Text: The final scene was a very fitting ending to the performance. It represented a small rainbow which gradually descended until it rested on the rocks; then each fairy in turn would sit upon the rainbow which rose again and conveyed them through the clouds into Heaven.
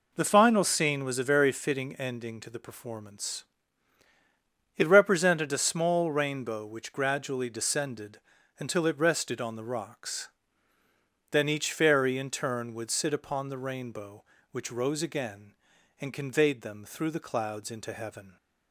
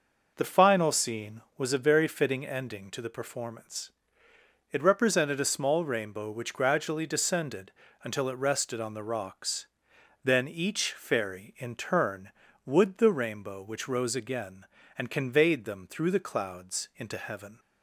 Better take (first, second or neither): first